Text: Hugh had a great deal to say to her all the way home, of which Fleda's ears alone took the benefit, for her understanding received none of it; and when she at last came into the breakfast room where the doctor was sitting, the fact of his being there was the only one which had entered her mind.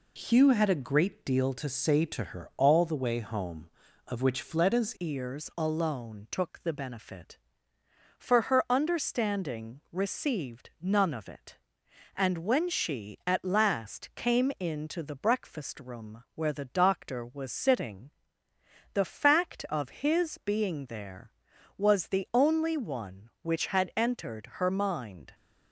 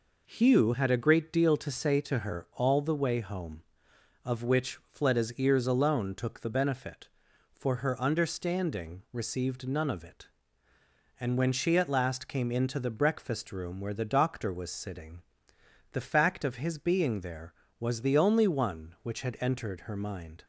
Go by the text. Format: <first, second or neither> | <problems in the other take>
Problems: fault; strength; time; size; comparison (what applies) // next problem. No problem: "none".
second | changes voice at "ears"; from 4.9 s on; 20.4 s long